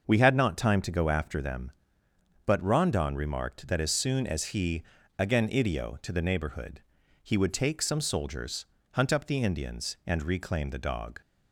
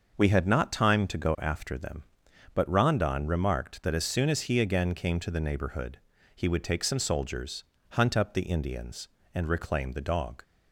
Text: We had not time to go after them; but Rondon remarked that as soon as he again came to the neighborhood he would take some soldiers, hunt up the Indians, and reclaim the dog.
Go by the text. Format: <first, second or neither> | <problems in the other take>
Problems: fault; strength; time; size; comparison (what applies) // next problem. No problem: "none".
second | starts louder than the rest; until 1.0 s; 6.5 dB; also in the second // pauses between "he" and "again"; slight; at 4.8 s; 0.34 s long // says "idio" for "came"; at 5.4 s // pauses between "neighborhood" and "he"; at 6.8 s; 0.42 s long; slight in the second